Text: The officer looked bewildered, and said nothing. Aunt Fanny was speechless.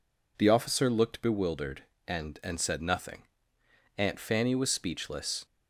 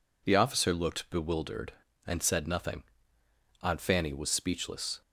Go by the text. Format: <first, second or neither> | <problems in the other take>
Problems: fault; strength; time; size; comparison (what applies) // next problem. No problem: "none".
second | says "and" twice; at 2.4 s